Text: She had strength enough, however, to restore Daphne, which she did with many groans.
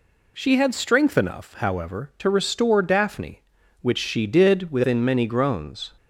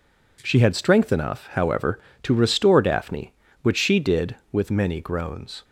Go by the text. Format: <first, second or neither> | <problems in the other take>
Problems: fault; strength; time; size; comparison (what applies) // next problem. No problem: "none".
second | says "within" for "with"; at 4.7 s